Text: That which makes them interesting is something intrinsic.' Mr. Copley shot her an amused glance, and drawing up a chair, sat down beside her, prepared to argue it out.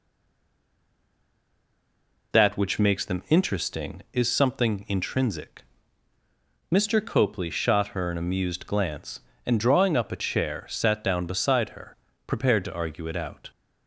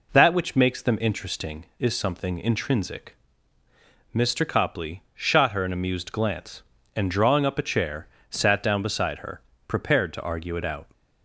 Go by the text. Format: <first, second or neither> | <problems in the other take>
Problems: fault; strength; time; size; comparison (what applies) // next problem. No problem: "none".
second | stays silent before the first word; until 2.3 s; 2.3 s long